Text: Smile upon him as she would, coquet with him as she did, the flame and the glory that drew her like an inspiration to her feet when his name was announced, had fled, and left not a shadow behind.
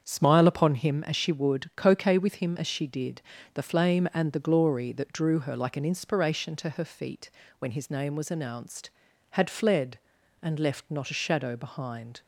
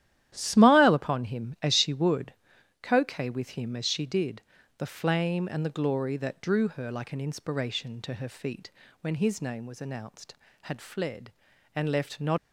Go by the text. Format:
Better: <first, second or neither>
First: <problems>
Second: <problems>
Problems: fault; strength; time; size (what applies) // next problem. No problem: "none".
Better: first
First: starts louder than the rest; strong; until 1.0 s; 7.5 dB // pauses between "feet" and "when"; slight; at 7.2 s; 0.30 s long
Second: starts louder than the rest; strong; until 1.3 s; 12 dB // pauses between "feet" and "when"; slight; at 8.7 s; 0.32 s long // stops before "a shadow behind"; at 12.3 s